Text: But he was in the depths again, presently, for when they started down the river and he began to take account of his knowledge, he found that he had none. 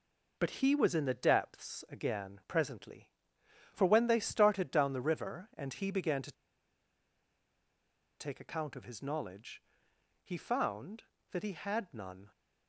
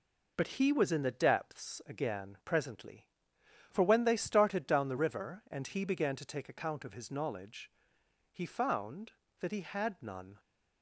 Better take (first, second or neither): second